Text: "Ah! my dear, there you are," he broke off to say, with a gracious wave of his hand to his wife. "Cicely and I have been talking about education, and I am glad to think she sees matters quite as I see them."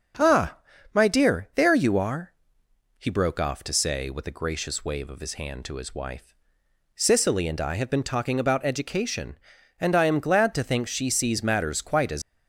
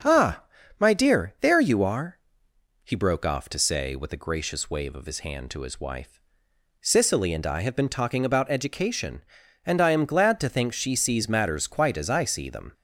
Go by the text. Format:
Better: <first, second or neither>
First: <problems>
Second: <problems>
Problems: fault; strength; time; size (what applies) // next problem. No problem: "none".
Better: second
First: starts louder than the rest; until 1.6 s; 6.5 dB // stops before "I see them"; at 12.2 s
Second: starts louder than the rest; until 1.4 s; 6.5 dB